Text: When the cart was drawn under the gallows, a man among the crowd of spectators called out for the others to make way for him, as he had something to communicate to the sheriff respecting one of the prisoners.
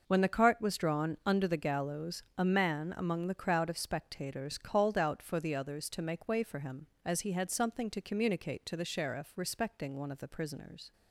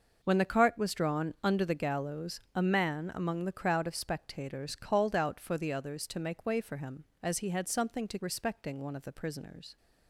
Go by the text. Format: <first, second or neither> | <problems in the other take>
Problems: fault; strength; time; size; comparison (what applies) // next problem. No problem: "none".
first | skips "communicate to the sheriff"; at 8.2 s